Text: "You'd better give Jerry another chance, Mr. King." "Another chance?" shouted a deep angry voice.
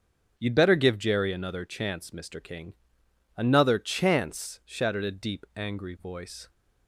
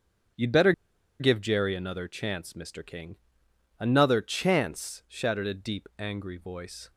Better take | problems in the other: first | starts louder than the rest; strong; until 1.8 s; 7.5 dB; also in the first // pauses between "better" and "give"; noticeable; at 0.7 s; 0.48 s long

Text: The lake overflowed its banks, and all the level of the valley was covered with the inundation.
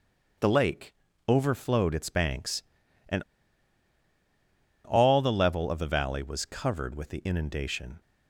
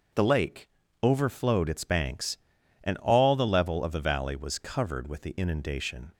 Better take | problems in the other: second | starts louder than the rest; until 1.7 s; 6 dB; noticeable in the second // pauses between "lake" and "overflowed"; slight; at 0.9 s; 0.34 s long; slight in the second // pauses between "and" and "all"; strong; at 3.2 s; 1.6 s long

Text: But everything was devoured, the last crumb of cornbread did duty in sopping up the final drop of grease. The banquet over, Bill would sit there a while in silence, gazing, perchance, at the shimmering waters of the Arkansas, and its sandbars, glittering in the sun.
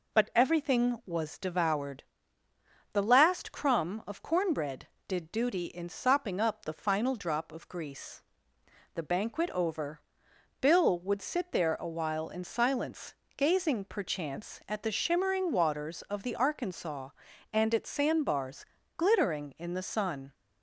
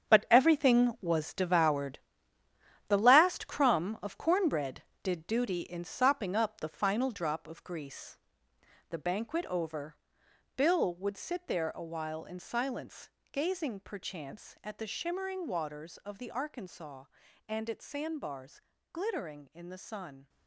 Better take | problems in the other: first | gets quieter; strong; throughout; 11 dB

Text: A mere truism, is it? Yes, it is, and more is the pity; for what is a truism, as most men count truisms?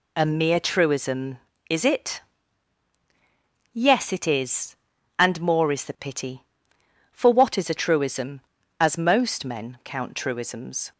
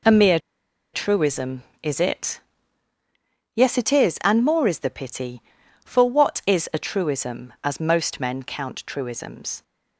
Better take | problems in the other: first | pauses between "mere" and "truism"; noticeable; at 0.3 s; 0.55 s long

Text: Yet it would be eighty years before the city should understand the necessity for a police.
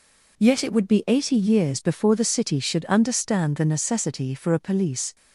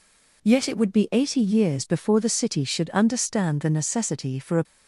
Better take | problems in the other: first | stops before "police"; at 4.6 s

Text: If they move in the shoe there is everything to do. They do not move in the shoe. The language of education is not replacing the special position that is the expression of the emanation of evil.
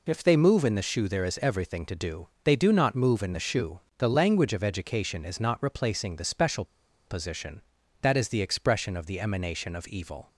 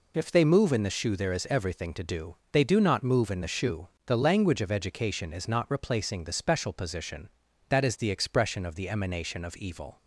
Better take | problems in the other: second | pauses between "special" and "position"; at 6.6 s; 0.43 s long

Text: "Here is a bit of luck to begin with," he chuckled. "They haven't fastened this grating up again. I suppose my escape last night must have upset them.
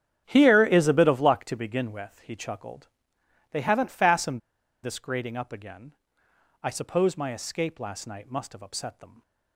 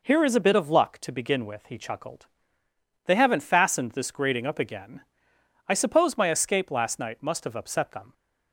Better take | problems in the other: second | starts louder than the rest; strong; until 1.2 s; 9.5 dB // pauses between "fastened" and "this"; at 4.4 s; 0.43 s long

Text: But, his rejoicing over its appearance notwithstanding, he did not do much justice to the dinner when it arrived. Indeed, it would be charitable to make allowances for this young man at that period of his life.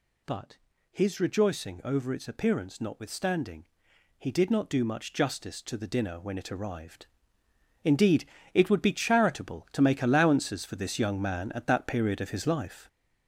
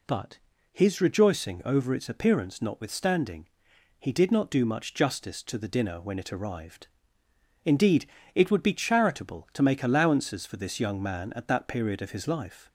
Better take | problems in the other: second | gets louder; throughout; 6.5 dB

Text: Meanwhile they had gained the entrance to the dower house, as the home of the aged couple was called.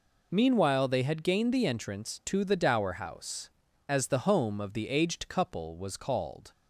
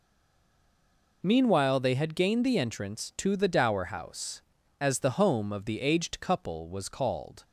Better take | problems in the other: first | stays silent before the first word; noticeable; until 1.2 s; 1.2 s long

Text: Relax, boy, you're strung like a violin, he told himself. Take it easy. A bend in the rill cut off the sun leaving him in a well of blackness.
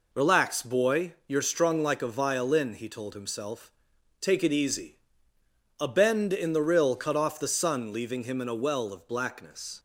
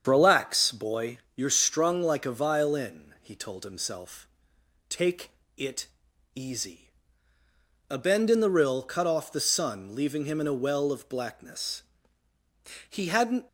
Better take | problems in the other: first | starts louder than the rest; strong; until 1.0 s; 7.5 dB // pauses between "Take" and "it"; slight; at 5.2 s; 0.26 s long // pauses between "it" and "easy"; noticeable; at 5.8 s; 0.48 s long // goes on to say "He hadn't"; from 12.8 s on; 0.58 s long

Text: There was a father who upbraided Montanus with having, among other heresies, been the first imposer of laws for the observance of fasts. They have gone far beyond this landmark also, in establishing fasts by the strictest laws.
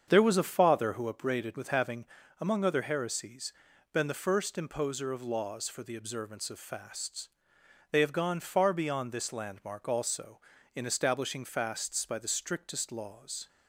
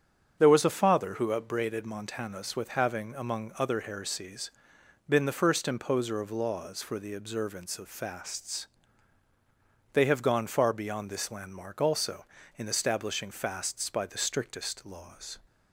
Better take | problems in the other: second | starts louder than the rest; strong; until 1.0 s; 7 dB; strong in the second // skips "Montanus"; at 1.5 s

